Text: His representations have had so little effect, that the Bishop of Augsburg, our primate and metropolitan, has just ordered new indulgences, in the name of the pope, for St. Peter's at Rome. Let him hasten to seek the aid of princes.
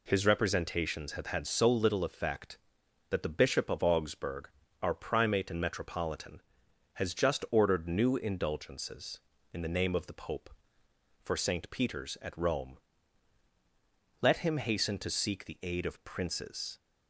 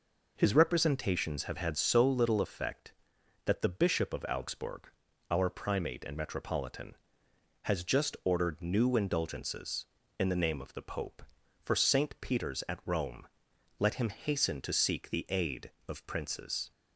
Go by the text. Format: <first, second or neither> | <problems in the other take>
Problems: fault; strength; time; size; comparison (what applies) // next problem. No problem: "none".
neither | none